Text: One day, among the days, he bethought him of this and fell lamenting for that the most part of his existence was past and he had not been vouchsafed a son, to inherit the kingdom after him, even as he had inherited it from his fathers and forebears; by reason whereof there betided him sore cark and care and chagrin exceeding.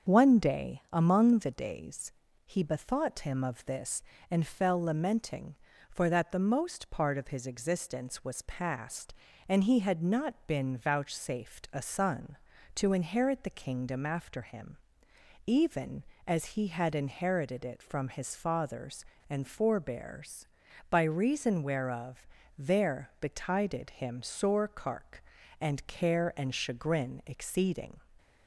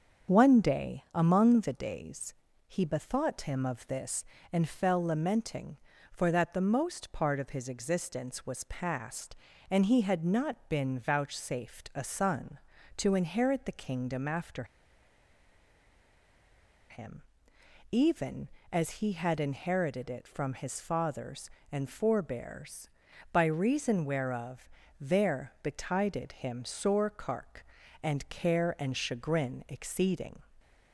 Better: first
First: starts louder than the rest; until 1.1 s; 7 dB // pauses between "whereof" and "there"; slight; at 22.2 s; 0.32 s long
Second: starts louder than the rest; until 1.3 s; 7 dB // pauses between "after" and "him"; strong; at 14.6 s; 2.2 s long // pauses between "whereof" and "there"; slight; at 24.6 s; 0.32 s long

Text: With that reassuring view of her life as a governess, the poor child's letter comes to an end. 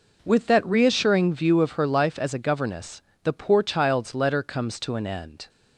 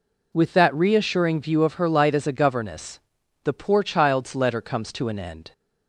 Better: first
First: none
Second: says "light" for "life"; at 1.9 s

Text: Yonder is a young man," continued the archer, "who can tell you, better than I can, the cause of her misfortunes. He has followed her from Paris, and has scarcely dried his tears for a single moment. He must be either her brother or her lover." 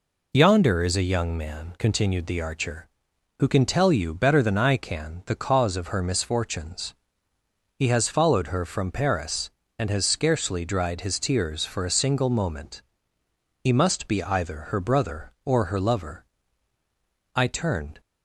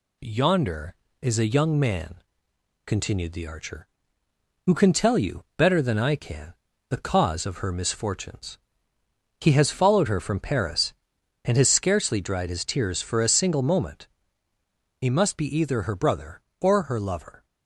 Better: second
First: goes on to say "I turned"; noticeable; from 17.3 s on; 0.64 s long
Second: none

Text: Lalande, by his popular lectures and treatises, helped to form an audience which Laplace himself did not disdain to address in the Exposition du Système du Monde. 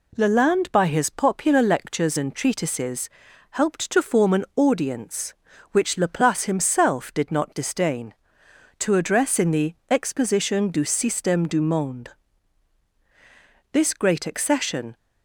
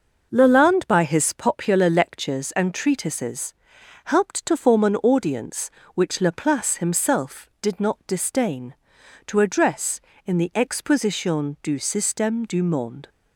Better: second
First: goes on to say "This great accession"; noticeable; from 13.7 s on; 1.2 s long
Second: none

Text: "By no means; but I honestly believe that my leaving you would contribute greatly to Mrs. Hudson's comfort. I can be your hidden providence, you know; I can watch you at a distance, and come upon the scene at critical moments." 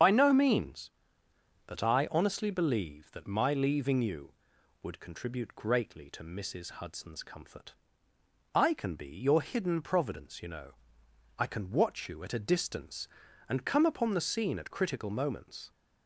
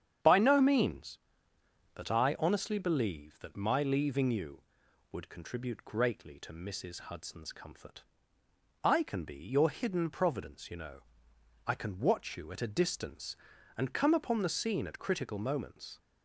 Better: second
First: loses the start of "By"; at 0.0 s; 55 ms // starts louder than the rest; strong; until 1.7 s; 7.5 dB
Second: starts louder than the rest; strong; until 2.0 s; 8.5 dB

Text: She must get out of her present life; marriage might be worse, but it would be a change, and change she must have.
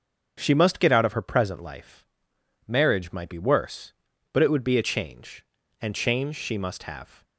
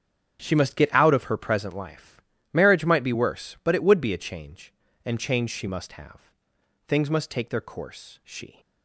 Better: first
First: starts louder than the rest; until 1.3 s; 6.5 dB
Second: starts louder than the rest; strong; until 1.4 s; 8 dB // goes on to say "Things must take their course she"; strong; from 6.8 s on; 1.7 s long

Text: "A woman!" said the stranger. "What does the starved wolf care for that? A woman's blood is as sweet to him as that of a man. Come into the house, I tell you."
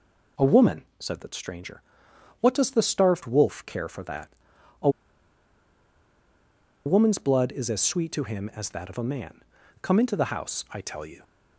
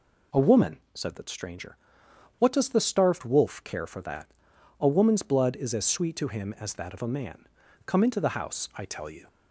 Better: second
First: pauses between "A" and "woman's"; strong; at 4.8 s; 1.9 s long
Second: none

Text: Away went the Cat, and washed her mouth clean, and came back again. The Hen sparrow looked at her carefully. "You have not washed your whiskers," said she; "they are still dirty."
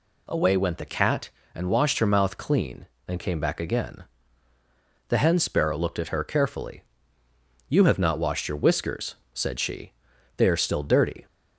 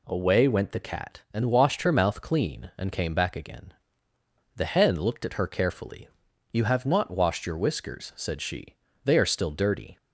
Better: first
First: none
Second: skips "sparrow"; at 4.9 s

